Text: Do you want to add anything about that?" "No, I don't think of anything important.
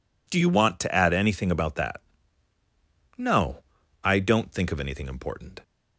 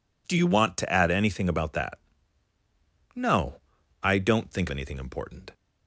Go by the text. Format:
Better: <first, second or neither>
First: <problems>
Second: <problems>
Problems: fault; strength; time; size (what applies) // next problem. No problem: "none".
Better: first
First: none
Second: skips "of"; at 4.6 s